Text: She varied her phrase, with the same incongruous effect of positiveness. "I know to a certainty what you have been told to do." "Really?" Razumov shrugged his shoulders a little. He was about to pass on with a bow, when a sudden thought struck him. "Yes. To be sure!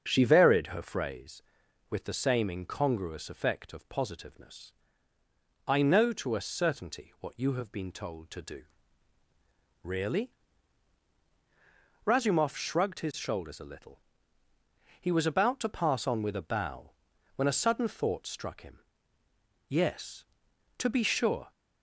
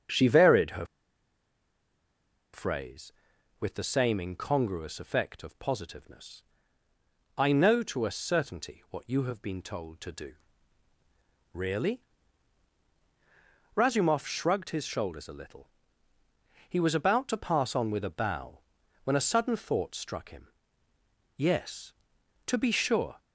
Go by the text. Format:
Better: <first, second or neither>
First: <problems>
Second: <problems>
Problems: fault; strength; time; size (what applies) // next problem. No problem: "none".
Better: first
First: starts louder than the rest; until 1.0 s; 7 dB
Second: starts louder than the rest; until 2.8 s; 7 dB // pauses between "her" and "phrase"; strong; at 0.8 s; 1.6 s long